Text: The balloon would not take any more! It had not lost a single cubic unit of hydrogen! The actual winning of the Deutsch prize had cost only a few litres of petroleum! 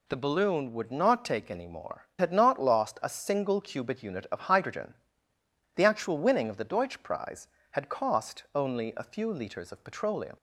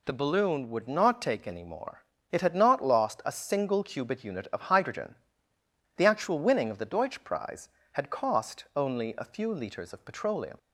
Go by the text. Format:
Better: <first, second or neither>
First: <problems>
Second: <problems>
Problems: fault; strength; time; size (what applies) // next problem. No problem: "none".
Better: second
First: skips "It"; at 2.1 s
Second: none